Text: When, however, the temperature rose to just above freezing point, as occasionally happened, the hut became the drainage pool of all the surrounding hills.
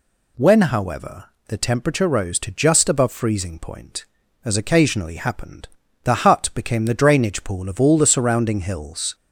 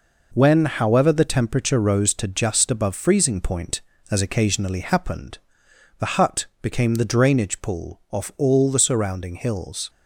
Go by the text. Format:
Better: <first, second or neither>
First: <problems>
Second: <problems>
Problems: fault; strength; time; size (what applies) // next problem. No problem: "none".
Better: first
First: none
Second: pauses between "hut" and "became"; slight; at 6.4 s; 0.16 s long // says "off" for "of"; at 8.1 s